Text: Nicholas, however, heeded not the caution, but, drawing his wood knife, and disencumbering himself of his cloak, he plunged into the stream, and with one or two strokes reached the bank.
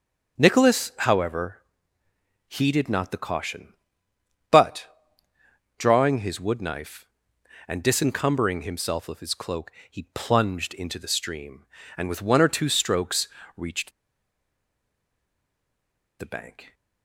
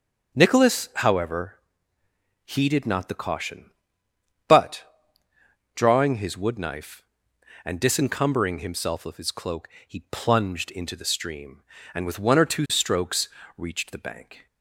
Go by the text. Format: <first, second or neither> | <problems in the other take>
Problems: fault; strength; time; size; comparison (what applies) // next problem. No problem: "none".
second | starts louder than the rest; strong; until 1.4 s; 7.5 dB; strong in the second // pauses between "strokes" and "reached"; slight; at 13.2 s; 0.26 s long; slight in the second // pauses between "reached" and "the"; strong; at 13.9 s; 2.2 s long